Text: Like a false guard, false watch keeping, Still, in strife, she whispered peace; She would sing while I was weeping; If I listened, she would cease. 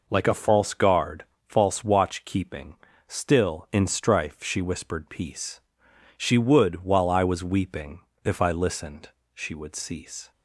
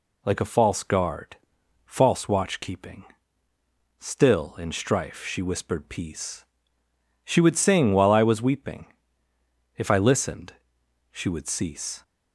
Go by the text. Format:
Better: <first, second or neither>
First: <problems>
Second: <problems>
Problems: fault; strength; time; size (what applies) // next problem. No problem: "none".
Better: second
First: skips "sing"; at 6.8 s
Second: none